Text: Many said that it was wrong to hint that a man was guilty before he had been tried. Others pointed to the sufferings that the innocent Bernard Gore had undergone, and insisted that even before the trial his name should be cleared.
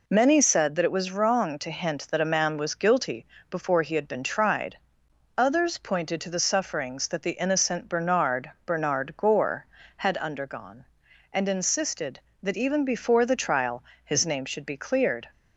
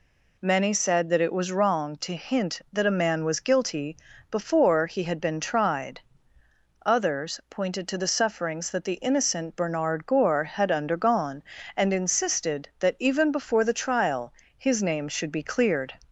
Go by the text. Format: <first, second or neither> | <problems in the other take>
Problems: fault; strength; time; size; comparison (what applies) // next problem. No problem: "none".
second | pauses between "guilty" and "before"; slight; at 3.2 s; 0.24 s long; slight in the second // says "Bernard" twice; at 8.6 s // pauses between "trial" and "his"; slight; at 13.8 s; 0.22 s long; slight in the second